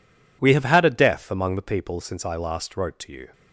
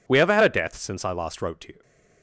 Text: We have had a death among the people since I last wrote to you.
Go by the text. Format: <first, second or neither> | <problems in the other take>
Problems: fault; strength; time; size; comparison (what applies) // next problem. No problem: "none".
first | skips "among the people"; at 0.7 s